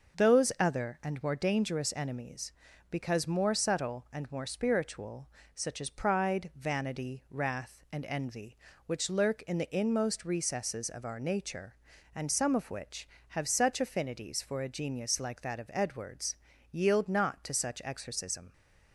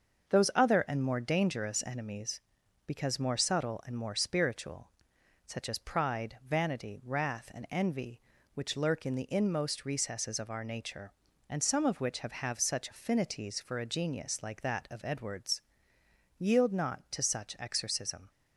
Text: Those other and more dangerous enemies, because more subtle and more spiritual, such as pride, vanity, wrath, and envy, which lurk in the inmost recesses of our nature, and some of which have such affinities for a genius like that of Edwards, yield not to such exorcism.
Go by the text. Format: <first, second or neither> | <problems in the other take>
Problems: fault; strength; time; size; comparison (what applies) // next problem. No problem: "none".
first | starts louder than the rest; until 1.4 s; 6.5 dB; noticeable in the first // says "have" twice; at 12.3 s